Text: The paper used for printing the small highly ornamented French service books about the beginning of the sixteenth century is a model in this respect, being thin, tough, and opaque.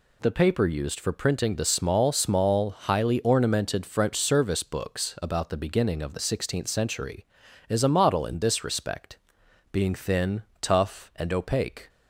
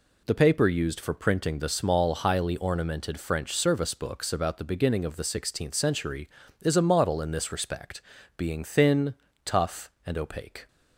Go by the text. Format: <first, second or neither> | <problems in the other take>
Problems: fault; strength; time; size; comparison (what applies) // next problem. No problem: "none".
second | says "small" twice; at 2.1 s